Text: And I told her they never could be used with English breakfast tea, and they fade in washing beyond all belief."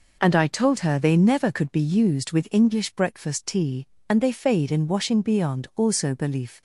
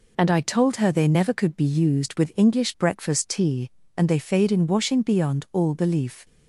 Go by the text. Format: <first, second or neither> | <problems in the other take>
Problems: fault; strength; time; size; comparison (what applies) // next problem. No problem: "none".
second | says "also" for "all"; at 5.7 s